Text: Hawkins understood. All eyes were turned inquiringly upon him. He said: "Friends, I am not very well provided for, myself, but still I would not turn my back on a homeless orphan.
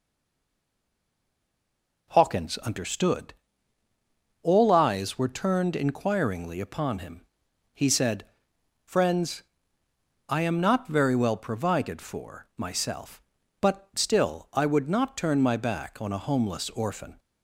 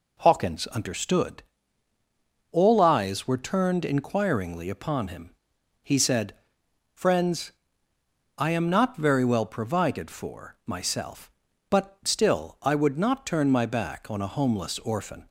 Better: second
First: stays silent before the first word; noticeable; until 2.0 s; 2.0 s long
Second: none

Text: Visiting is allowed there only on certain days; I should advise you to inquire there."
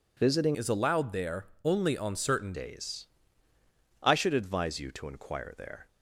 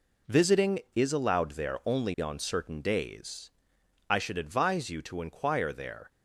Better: second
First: changes voice from "is" to "certain"; from 0.5 to 2.5 s; 2.0 s long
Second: none

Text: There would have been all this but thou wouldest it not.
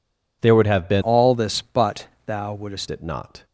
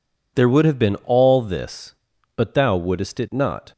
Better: second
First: changes voice from "all" to "wouldest"; from 1.0 to 2.8 s; 1.8 s long // pauses between "but" and "thou"; slight; at 2.0 s; 0.20 s long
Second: none

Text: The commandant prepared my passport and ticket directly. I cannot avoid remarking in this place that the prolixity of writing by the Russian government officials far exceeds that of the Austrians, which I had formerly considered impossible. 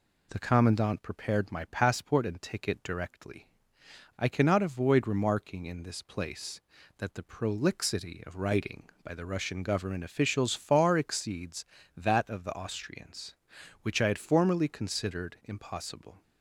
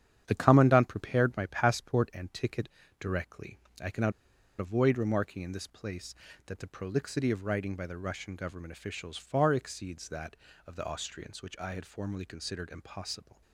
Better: first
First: none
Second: starts louder than the rest; strong; until 1.2 s; 9.5 dB // pauses between "ticket" and "directly"; slight; at 2.6 s; 0.32 s long // pauses between "cannot" and "avoid"; noticeable; at 4.1 s; 0.48 s long

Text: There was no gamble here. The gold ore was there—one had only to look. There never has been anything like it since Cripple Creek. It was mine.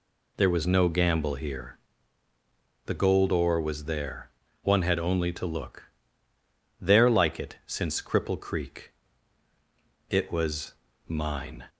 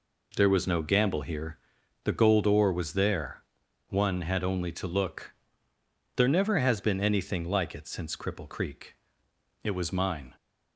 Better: second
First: skips "never has been anything"; at 7.1 s // pauses between "was" and "mine"; slight; at 10.7 s; 0.34 s long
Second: none

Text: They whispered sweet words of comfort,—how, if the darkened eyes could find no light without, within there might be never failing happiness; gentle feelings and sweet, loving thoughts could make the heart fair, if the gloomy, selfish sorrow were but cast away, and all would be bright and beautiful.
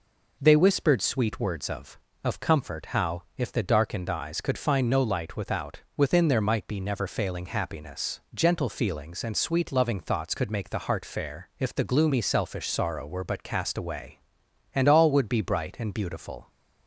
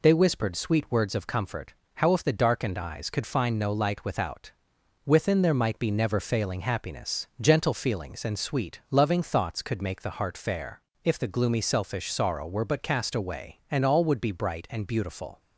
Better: second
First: says "of" twice; at 2.2 s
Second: none

